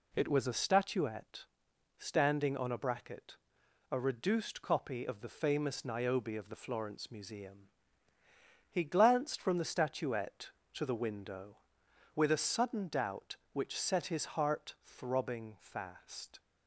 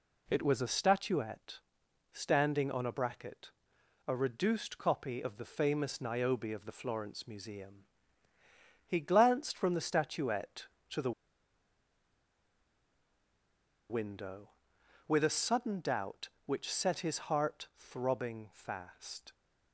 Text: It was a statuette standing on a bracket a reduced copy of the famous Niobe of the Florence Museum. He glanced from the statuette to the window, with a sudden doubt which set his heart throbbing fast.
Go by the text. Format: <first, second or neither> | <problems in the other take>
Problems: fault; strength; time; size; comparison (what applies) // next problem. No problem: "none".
first | pauses between "statuette" and "standing"; noticeable; at 1.5 s; 0.52 s long; noticeable in the first // pauses between "bracket" and "a"; noticeable; at 3.5 s; 0.58 s long; noticeable in the first // pauses between "the" and "window"; strong; at 11.1 s; 2.7 s long